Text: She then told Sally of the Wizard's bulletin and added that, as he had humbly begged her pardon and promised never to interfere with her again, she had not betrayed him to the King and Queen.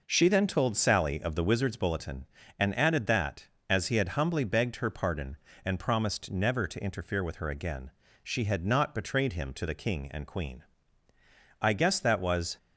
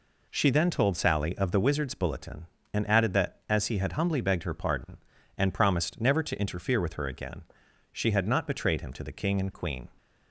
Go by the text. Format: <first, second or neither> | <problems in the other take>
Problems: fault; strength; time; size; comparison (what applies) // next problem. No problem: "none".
second | goes on to say "I guess that was"; noticeable; from 11.6 s on; 0.96 s long